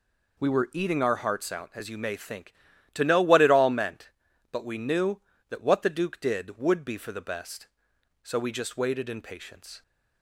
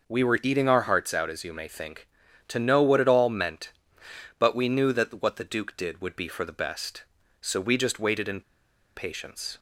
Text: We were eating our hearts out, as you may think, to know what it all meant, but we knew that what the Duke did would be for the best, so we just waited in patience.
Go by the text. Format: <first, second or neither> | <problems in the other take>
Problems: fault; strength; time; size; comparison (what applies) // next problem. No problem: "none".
first | pauses between "in" and "patience"; noticeable; at 8.4 s; 0.54 s long